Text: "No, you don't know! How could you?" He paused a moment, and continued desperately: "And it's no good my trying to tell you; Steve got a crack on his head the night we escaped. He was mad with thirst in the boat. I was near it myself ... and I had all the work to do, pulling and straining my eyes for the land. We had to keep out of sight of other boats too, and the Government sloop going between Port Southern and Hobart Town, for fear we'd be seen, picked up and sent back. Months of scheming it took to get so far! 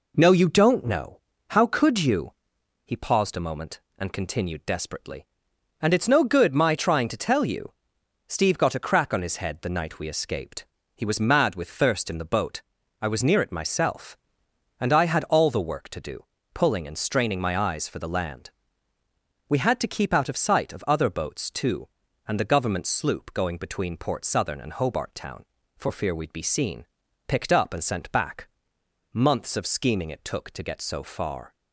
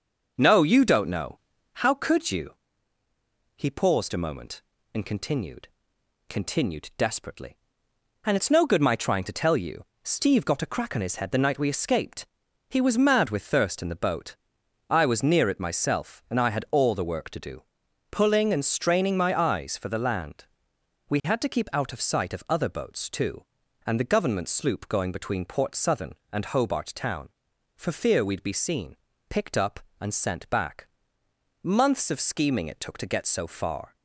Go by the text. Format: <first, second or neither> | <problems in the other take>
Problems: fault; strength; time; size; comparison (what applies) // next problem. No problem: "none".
first | says "continued" twice; at 6.2 s